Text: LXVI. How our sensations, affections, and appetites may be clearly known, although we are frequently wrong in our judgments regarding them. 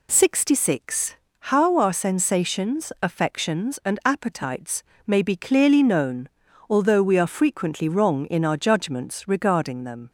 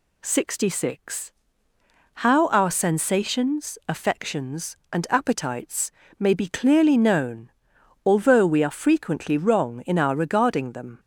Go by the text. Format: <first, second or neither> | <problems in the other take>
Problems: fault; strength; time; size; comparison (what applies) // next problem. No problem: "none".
first | pauses between "appetites" and "may"; slight; at 5.9 s; 0.26 s long; slight in the first // skips "judgments"; at 10.1 s